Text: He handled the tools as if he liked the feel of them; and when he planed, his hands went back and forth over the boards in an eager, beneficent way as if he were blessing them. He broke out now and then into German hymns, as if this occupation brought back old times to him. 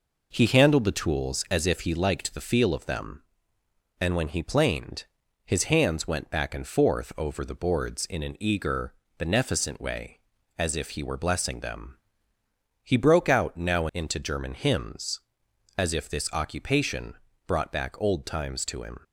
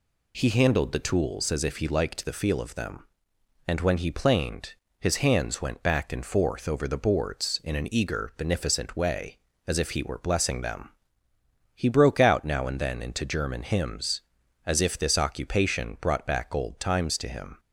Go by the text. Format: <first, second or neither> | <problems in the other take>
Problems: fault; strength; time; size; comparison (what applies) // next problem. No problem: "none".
second | skips "and then"; at 13.9 s // pauses between "occupation" and "brought"; slight; at 17.1 s; 0.32 s long